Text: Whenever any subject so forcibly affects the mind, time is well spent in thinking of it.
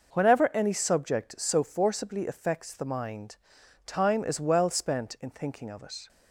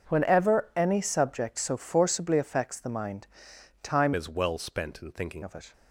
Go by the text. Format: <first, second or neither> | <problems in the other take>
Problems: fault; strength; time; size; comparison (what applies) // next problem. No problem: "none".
first | starts louder than the rest; until 1.1 s; 6 dB // changes voice from "is" to "thinking"; from 4.1 to 5.4 s; 1.3 s long